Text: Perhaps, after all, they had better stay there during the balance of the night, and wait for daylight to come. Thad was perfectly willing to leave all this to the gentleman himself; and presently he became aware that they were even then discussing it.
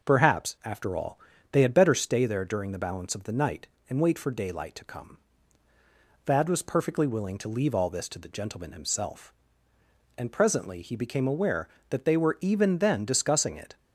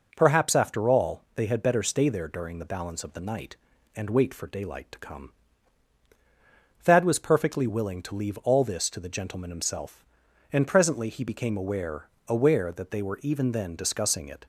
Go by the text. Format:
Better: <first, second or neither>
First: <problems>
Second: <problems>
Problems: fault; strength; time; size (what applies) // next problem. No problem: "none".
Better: first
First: none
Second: says "aware" twice; at 12.2 s